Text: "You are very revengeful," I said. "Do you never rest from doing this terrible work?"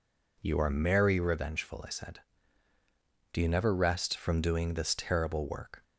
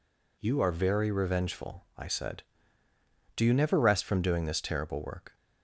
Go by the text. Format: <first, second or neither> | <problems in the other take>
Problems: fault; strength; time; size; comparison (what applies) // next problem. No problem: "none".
second | says "merry" for "very"; at 0.7 s